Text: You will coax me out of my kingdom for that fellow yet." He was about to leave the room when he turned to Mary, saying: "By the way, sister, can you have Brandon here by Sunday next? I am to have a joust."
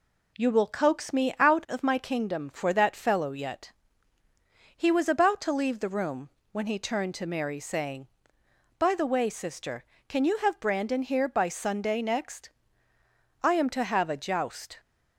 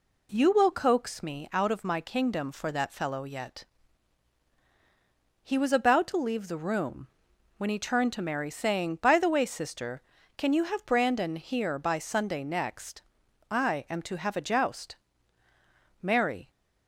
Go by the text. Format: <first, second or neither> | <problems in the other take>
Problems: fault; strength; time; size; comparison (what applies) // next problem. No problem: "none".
first | pauses between "room" and "when"; noticeable; at 7.0 s; 0.50 s long; slight in the first // goes on to say "Mary"; from 15.9 s on; 0.50 s long